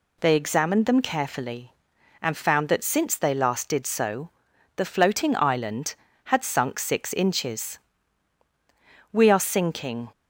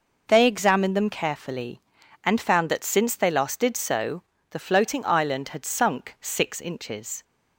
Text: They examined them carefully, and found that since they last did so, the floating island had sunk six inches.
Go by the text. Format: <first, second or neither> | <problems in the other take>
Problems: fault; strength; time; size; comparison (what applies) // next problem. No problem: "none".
second | goes on to say "We are sinking"; noticeable; from 9.1 s on; 0.96 s long